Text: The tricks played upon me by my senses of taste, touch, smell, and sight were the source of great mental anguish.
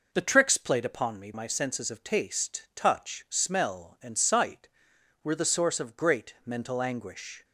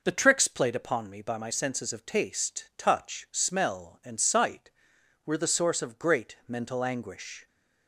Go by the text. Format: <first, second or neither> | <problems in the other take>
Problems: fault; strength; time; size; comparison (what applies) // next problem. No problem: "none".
second | skips "by"; at 1.3 s